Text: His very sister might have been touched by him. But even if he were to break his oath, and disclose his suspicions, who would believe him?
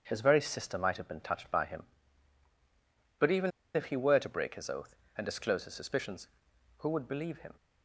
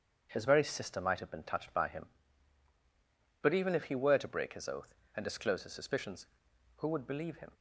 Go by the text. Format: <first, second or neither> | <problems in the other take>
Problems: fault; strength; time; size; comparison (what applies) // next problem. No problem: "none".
second | starts louder than the rest; strong; until 1.0 s; 7.5 dB; strong in the second // pauses between "even" and "if"; slight; at 3.5 s; 0.25 s long